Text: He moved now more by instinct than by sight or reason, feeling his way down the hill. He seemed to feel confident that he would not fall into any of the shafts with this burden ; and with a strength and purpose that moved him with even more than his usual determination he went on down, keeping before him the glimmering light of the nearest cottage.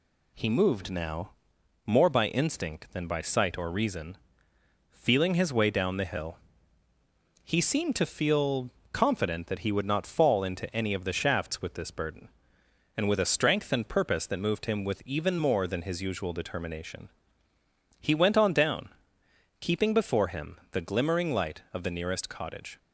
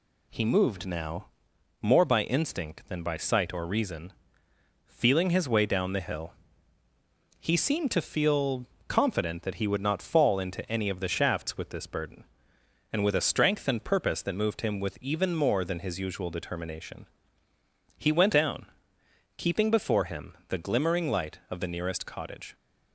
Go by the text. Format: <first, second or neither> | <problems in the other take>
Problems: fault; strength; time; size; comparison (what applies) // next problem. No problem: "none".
first | pauses between "now" and "more"; noticeable; at 1.2 s; 0.54 s long; noticeable in the first // pauses between "feel" and "confident"; slight; at 8.6 s; 0.24 s long; slight in the first // pauses between "determination" and "he"; noticeable; at 17.0 s; 0.90 s long; noticeable in the first // skips "on"; at 18.3 s